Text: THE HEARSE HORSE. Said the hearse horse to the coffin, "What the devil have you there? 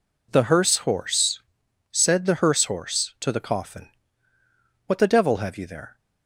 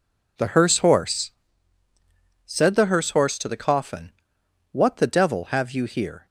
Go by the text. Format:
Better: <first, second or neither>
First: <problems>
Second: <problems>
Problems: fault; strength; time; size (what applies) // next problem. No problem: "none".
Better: first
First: none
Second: says "here" for "there"; at 5.8 s